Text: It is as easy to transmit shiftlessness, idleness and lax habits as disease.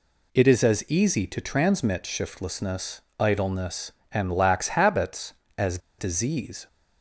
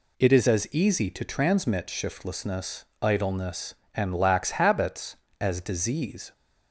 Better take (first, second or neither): second